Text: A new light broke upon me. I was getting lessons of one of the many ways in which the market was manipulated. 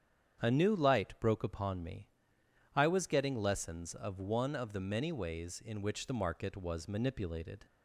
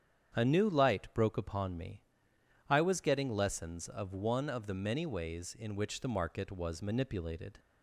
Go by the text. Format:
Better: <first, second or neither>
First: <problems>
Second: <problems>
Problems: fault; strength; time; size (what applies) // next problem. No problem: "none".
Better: neither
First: starts louder than the rest; strong; until 1.4 s; 8.5 dB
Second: starts louder than the rest; strong; until 1.3 s; 8.5 dB